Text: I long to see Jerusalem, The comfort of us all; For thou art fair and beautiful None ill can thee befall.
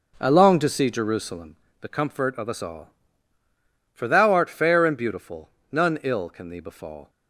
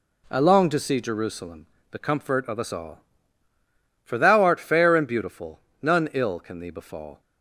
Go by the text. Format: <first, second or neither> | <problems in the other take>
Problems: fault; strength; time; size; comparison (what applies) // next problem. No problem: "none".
second | starts louder than the rest; noticeable; until 1.5 s; 5.5 dB // pauses between "beautiful" and "None"; slight; at 5.4 s; 0.22 s long; slight in the second